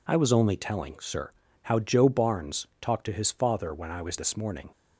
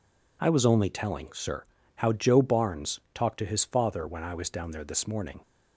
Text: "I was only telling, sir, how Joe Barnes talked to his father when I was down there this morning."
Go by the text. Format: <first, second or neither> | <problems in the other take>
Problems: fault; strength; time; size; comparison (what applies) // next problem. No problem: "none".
second | skips "down there"; at 4.1 s